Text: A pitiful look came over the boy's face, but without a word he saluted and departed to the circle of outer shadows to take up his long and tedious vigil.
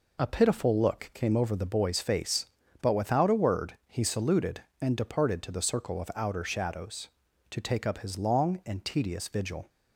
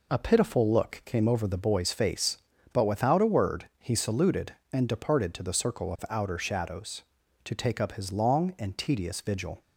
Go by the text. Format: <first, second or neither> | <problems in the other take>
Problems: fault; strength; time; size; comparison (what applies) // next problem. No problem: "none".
neither | none